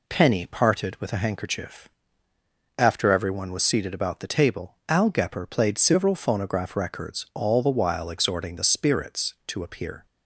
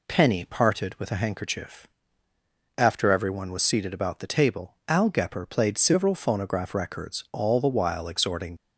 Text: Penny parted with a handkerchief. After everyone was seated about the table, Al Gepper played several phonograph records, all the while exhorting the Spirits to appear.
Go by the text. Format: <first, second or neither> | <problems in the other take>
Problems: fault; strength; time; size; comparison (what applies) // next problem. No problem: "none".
first | stops before "the Spirits to appear"; at 8.5 s